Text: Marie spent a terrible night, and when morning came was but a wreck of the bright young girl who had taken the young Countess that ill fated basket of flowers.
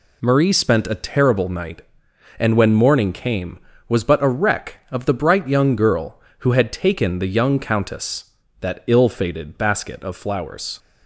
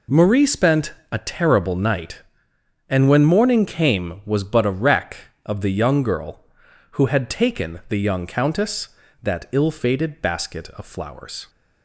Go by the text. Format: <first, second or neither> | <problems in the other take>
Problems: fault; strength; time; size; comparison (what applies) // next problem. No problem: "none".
first | pauses between "spent" and "a"; slight; at 0.9 s; 0.18 s long // skips "bright"; at 5.6 s